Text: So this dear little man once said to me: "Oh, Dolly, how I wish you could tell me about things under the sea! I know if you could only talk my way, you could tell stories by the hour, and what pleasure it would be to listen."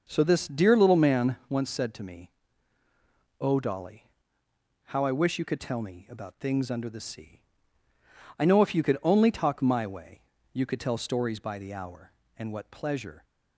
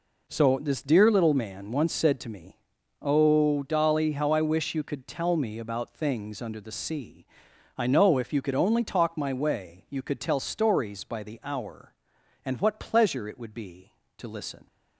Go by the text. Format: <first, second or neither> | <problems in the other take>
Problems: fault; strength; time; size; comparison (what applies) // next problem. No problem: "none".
second | stops before "it would be to listen"; at 13.2 s